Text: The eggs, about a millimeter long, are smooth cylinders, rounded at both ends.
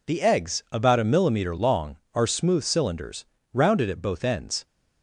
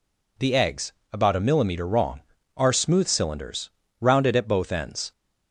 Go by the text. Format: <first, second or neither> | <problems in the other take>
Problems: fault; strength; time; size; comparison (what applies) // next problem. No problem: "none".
first | says "wrong" for "long"; at 1.8 s